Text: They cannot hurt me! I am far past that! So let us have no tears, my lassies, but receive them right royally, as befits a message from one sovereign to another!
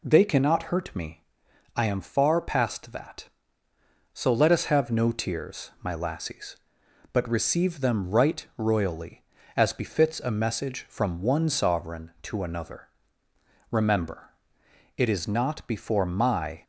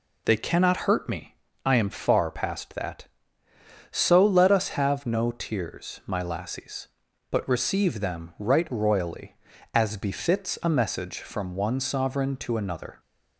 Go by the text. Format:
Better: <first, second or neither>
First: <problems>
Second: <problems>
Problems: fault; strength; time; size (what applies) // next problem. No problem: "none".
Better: second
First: goes on to say "Remember it is not before my"; strong; from 13.7 s on; 2.9 s long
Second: none